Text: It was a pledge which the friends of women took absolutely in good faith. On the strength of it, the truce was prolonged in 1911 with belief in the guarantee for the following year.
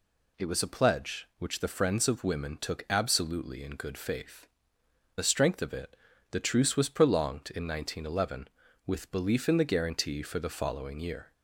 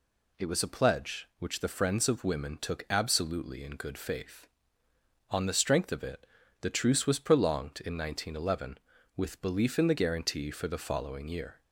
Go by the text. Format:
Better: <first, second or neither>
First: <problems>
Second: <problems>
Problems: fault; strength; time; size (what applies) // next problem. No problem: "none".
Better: second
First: skips "On"; at 4.8 s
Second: none